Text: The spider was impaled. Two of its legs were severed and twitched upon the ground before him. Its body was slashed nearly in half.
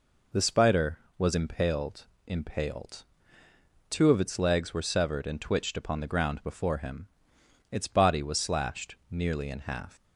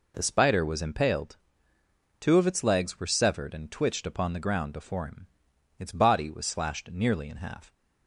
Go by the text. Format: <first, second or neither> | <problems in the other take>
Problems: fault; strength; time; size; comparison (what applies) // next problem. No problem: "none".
second | says "impaled" twice; at 2.2 s